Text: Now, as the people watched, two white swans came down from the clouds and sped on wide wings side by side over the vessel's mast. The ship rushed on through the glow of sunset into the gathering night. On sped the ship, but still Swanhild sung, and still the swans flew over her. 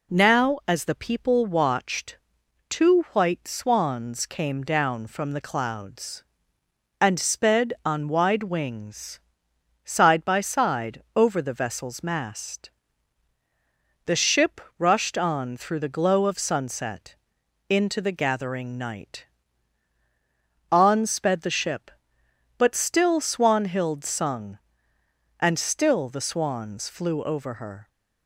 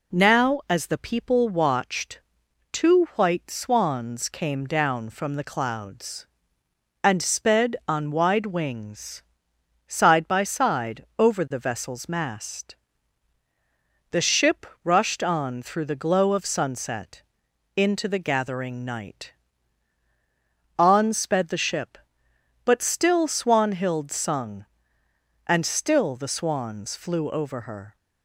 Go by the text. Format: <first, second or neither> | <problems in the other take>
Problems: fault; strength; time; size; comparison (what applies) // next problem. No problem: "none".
neither | pauses between "wings" and "side"; noticeable; the same in both // pauses between "ship" and "rushed"; slight; the same in both // pauses between "sunset" and "into"; noticeable; the same in both